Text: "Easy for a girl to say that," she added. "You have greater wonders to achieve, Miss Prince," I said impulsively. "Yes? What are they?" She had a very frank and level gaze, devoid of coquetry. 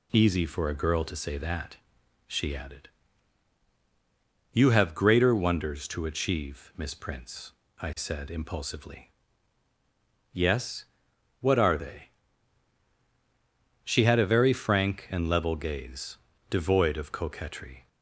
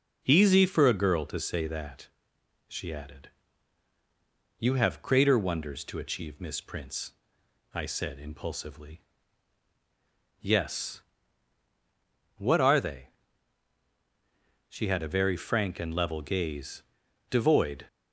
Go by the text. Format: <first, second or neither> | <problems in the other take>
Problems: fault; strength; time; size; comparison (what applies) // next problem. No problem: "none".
first | stops before "of coquetry"; at 17.8 s